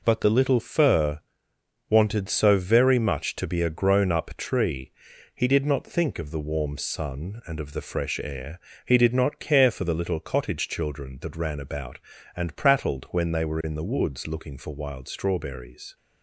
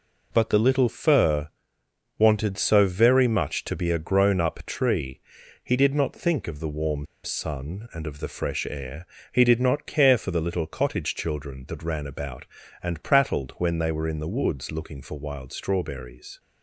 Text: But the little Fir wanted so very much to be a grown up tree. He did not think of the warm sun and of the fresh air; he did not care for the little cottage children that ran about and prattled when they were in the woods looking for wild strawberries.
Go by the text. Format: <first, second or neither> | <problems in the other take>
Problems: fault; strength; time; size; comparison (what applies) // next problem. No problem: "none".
first | pauses between "Fir" and "wanted"; noticeable; at 1.4 s; 0.68 s long; noticeable in the first // pauses between "warm" and "sun"; slight; at 7.0 s; 0.18 s long